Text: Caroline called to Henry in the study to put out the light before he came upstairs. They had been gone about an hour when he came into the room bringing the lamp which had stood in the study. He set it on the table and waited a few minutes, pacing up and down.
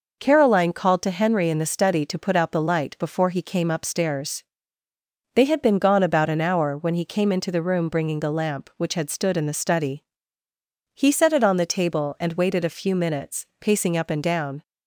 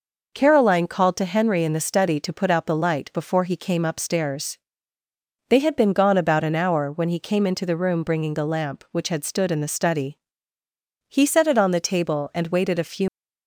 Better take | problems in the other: first | stops before "minutes pacing up and down"; at 13.0 s

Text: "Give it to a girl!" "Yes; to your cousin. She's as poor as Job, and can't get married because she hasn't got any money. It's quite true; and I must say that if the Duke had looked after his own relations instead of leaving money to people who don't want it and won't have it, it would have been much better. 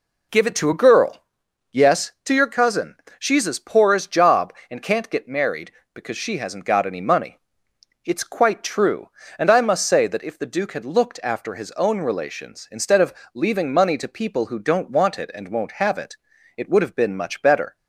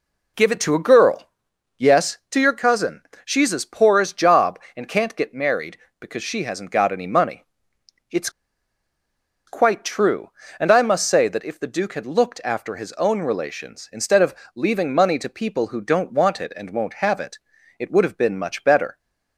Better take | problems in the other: first | pauses between "It's" and "quite"; at 8.2 s; 1.1 s long // pauses between "of" and "leaving"; slight; at 14.3 s; 0.18 s long; slight in the first

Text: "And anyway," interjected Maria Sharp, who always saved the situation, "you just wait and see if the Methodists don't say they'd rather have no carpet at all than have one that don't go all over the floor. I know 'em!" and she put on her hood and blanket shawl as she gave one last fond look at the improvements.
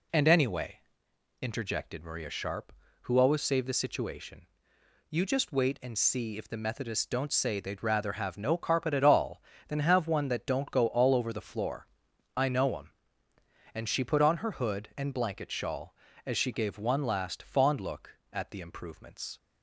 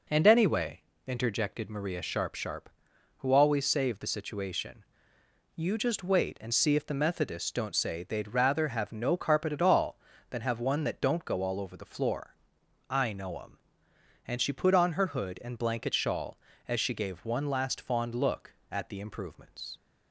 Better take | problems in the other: first | says "Sharp" twice; at 2.3 s

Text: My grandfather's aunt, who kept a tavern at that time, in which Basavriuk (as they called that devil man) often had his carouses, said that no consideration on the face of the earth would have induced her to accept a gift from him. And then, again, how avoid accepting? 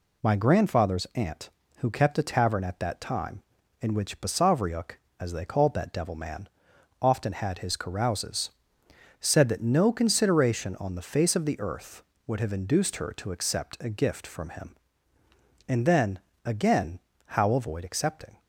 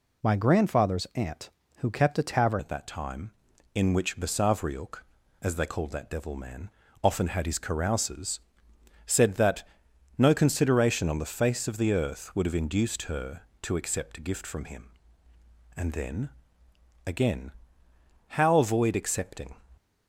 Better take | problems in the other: first | changes voice at "at"; from 2.5 s on; 17.0 s long // pauses between "that" and "no"; noticeable; at 9.6 s; 0.52 s long

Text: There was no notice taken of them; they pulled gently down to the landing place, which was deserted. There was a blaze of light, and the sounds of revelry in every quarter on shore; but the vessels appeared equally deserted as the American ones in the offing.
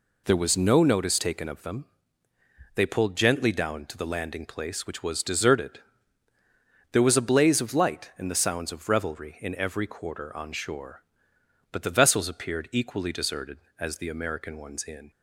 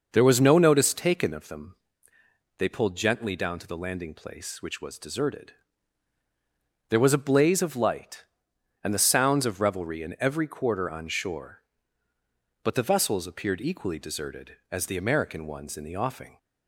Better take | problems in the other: second | stops before "the offing"; at 15.1 s

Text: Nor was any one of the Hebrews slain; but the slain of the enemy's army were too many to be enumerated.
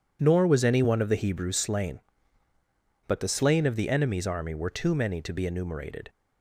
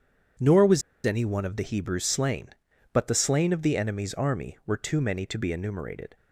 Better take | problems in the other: first | pauses between "was" and "any"; slight; at 0.8 s; 0.24 s long

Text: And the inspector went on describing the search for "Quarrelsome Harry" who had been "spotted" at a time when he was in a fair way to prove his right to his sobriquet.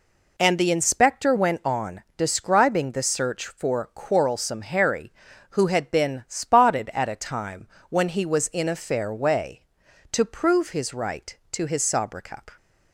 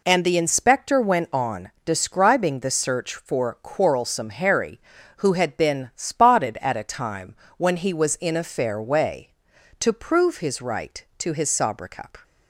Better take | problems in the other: neither | pauses between "time" and "when"; slight; the same in both

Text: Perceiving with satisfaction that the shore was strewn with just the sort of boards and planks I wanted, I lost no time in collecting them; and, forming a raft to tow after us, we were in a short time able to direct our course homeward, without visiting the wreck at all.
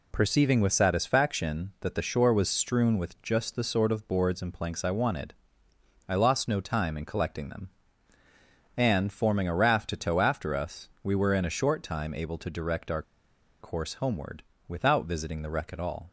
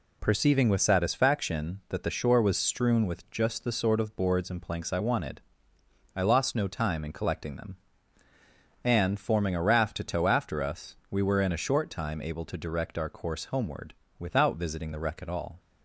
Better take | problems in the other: second | pauses between "our" and "course"; noticeable; at 13.0 s; 0.58 s long

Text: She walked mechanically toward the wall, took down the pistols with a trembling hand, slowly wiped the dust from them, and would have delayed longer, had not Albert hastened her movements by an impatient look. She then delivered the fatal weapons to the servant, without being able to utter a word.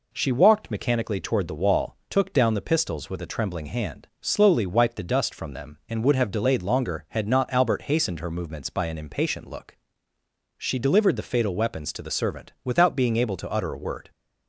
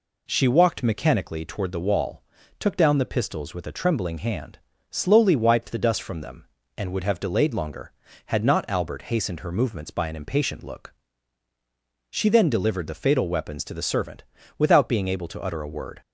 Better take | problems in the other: second | skips "then"; at 10.7 s

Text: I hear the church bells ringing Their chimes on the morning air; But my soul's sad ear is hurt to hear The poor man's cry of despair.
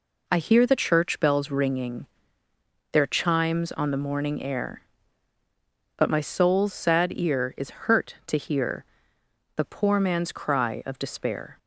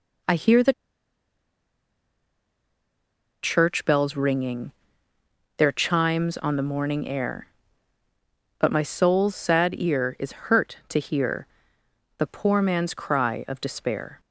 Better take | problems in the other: first | pauses between "the" and "church"; strong; at 0.7 s; 2.7 s long // pauses between "ringing" and "Their"; noticeable; at 4.7 s; 0.84 s long; noticeable in the first // pauses between "hear" and "The"; noticeable; at 11.4 s; 0.72 s long; noticeable in the first

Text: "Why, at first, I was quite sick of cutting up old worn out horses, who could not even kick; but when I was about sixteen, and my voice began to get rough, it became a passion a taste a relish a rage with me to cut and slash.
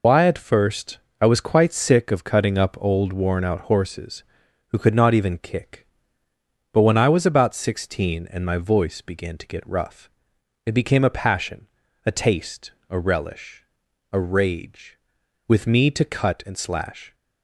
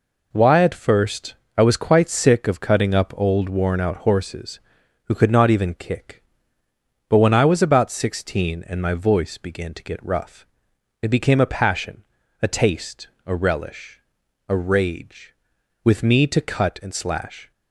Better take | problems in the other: second | loses the start of "Why"; at 0.0 s; 80 ms // pauses between "passion" and "a"; slight; at 11.6 s; 0.36 s long; slight in the second // pauses between "taste" and "a"; slight; at 12.7 s; 0.16 s long; slight in the second // pauses between "relish" and "a"; noticeable; at 13.6 s; 0.48 s long; noticeable in the second

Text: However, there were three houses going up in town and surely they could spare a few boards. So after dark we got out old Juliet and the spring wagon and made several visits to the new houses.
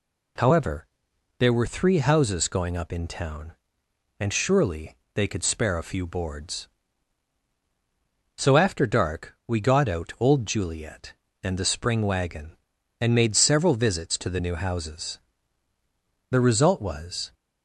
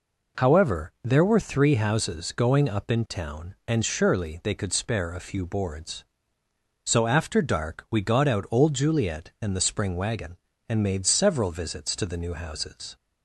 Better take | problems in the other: second | pauses between "surely" and "they"; slight; at 4.9 s; 0.20 s long // goes on to say "The result was"; noticeable; from 16.3 s on; 1.0 s long

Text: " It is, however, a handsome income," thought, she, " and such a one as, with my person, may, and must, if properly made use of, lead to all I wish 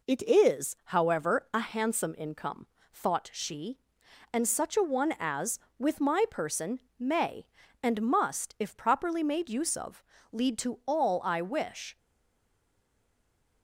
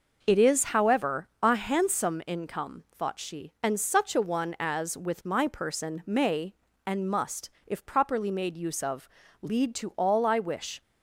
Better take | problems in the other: second | stays silent after the last word; noticeable; from 11.9 s on; 1.7 s long

